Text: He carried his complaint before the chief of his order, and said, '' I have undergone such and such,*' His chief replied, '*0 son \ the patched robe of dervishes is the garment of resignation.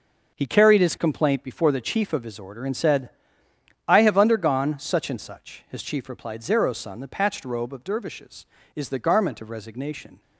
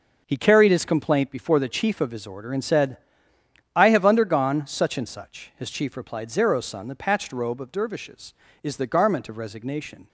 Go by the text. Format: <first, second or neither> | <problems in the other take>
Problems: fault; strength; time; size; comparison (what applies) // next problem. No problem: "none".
neither | none